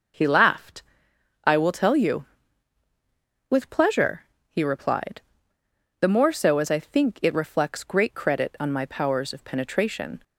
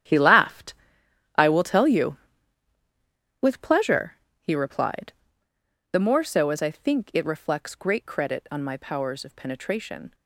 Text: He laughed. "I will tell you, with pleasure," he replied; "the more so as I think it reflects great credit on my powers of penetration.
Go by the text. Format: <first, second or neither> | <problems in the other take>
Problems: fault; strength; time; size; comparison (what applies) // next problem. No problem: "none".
first | gets quieter; strong; throughout; 12.5 dB